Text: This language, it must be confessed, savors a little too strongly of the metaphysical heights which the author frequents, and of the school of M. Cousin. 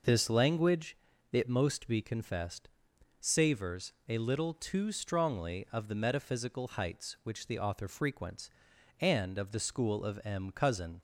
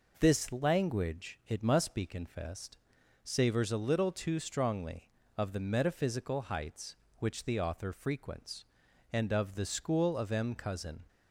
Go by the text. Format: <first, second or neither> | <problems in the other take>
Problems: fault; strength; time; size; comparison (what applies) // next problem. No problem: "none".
second | says "most" for "must"; at 1.4 s // pauses between "savors" and "a"; slight; at 3.9 s; 0.16 s long